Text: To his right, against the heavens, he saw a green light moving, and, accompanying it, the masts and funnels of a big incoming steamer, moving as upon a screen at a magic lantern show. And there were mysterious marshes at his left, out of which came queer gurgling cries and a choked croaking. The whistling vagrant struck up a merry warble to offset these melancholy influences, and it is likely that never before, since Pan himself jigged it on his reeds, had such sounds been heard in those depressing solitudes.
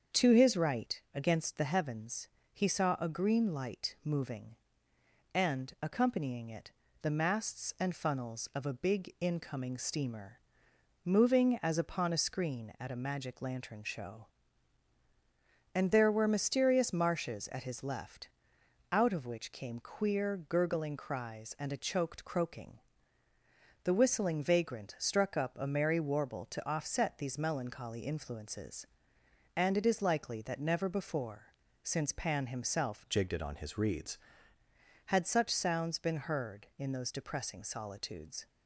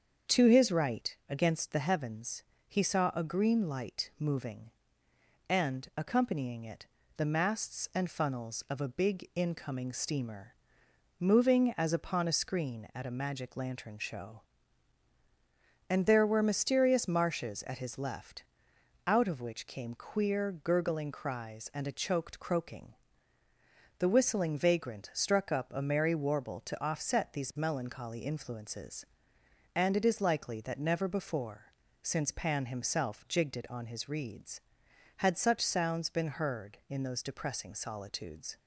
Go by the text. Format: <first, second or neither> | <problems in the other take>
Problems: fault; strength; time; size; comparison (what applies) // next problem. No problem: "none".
second | starts louder than the rest; until 1.2 s; 7 dB; also in the second // changes voice from "jigged" to "reeds"; from 33.0 to 34.1 s; 1.1 s long